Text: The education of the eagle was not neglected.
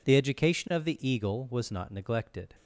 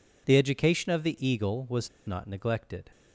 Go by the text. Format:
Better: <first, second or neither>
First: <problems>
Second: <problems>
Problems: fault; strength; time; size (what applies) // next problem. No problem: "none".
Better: first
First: none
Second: pauses between "was" and "not"; slight; at 1.8 s; 0.19 s long